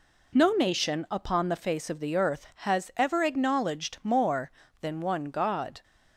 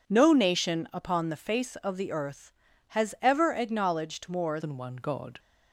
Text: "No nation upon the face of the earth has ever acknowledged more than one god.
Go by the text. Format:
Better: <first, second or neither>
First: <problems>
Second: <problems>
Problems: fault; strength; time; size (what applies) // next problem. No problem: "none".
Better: first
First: none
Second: changes voice at "than"; from 4.5 s on; 0.8 s long